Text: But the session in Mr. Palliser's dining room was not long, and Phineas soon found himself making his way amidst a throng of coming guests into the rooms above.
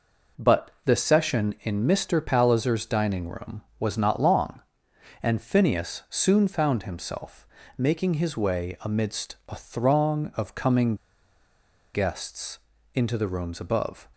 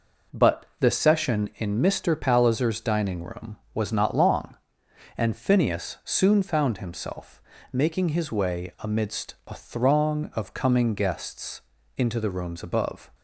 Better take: second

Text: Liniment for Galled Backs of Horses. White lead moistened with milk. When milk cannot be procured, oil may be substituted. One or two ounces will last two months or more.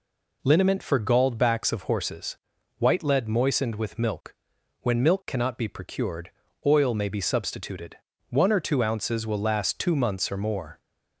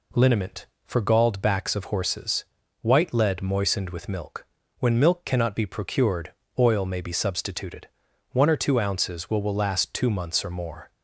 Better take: first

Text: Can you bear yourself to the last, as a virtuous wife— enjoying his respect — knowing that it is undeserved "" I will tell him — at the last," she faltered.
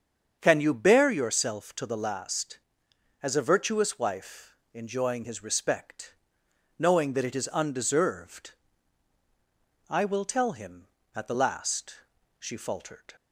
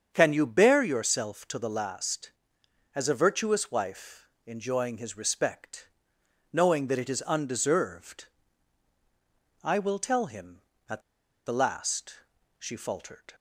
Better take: first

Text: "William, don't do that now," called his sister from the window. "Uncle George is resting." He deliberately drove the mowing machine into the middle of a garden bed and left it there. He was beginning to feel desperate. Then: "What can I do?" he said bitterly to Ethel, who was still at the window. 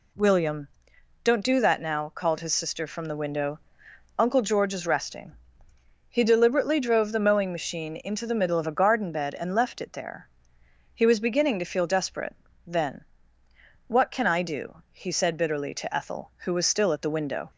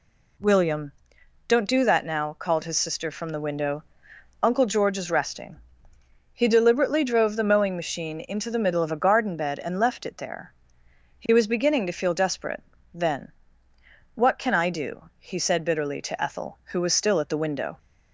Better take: neither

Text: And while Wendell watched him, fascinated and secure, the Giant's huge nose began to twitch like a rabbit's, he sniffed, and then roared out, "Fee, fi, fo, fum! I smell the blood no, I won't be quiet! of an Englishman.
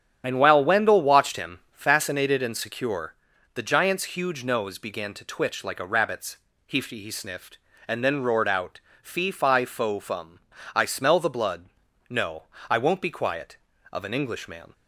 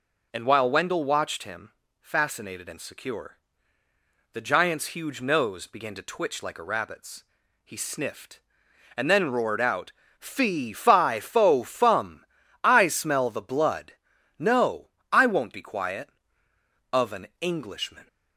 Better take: second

